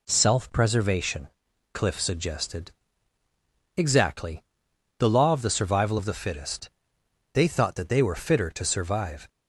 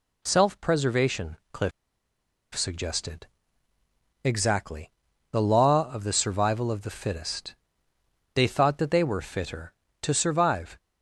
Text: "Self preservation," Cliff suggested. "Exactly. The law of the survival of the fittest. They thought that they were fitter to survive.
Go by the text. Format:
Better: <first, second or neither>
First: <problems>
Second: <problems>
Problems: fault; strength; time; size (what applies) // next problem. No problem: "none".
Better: first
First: none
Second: pauses between "Cliff" and "suggested"; noticeable; at 1.7 s; 0.84 s long